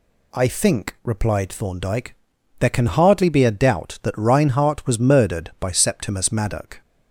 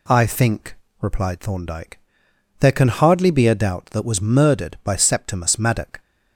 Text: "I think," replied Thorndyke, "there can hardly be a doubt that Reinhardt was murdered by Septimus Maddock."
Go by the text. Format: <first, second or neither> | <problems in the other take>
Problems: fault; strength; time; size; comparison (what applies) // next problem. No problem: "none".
first | skips "Reinhardt"; at 4.0 s